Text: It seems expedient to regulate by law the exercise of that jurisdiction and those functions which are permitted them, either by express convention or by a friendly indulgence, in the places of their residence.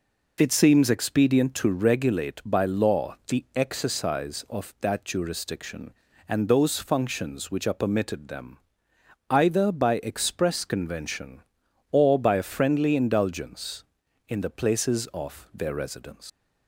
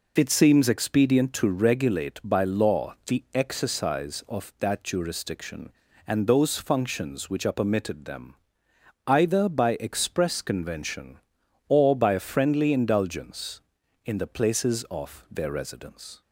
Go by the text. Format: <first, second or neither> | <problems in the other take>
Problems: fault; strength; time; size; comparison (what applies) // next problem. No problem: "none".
second | leaves "residence" unfinished; at 16.2 s; 140 ms